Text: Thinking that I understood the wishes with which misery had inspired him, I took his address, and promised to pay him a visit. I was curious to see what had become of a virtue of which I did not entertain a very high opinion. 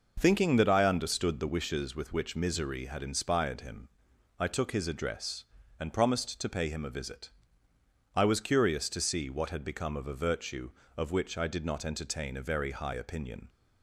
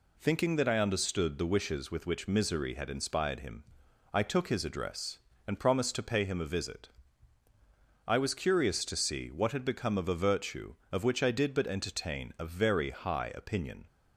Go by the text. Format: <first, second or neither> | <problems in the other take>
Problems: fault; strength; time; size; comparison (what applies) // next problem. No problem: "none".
first | says "but" for "not"; at 11.5 s